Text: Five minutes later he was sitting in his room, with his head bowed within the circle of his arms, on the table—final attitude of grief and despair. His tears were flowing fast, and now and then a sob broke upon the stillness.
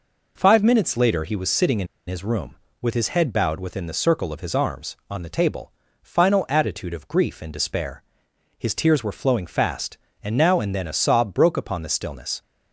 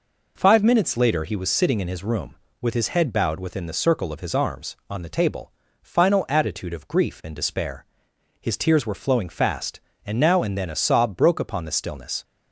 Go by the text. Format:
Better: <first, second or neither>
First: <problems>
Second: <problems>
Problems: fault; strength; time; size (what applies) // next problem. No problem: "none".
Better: second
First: pauses between "in" and "his"; slight; at 1.8 s; 0.22 s long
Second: none